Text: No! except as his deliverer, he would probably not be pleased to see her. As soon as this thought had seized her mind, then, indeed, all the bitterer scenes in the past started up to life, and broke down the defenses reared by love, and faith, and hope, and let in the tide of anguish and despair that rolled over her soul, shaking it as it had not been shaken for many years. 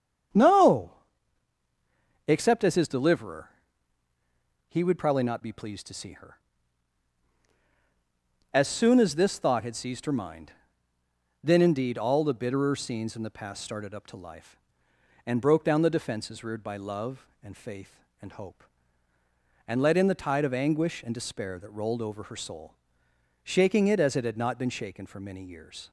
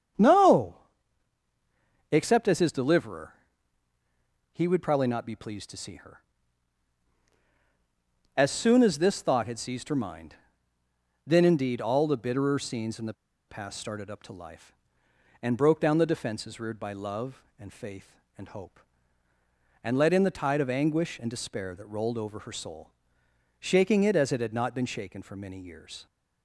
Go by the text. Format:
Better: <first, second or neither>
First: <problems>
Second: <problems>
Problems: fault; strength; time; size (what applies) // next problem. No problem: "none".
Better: first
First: starts louder than the rest; strong; until 2.6 s; 8 dB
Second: starts louder than the rest; strong; until 2.5 s; 8 dB // pauses between "the" and "past"; slight; at 13.1 s; 0.35 s long